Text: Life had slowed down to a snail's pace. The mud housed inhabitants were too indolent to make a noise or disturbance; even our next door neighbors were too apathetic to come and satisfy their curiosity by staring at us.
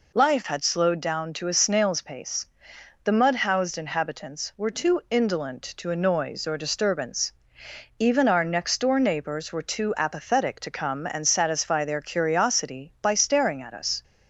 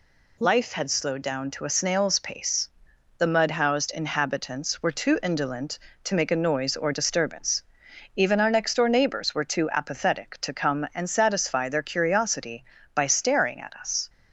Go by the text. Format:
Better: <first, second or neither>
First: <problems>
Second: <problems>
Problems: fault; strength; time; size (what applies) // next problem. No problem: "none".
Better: second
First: skips "make"; at 5.8 s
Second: none